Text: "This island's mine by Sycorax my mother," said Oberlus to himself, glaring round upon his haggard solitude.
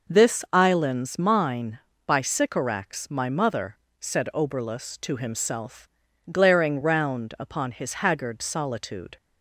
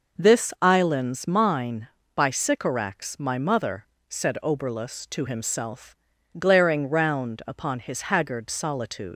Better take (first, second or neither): first